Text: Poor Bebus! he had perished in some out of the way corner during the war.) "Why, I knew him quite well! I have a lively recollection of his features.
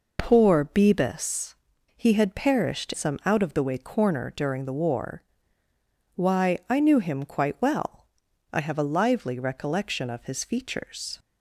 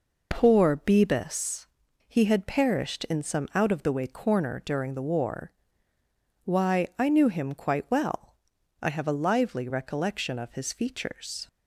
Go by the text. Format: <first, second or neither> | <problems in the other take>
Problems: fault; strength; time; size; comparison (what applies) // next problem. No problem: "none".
second | skips "in"; at 2.9 s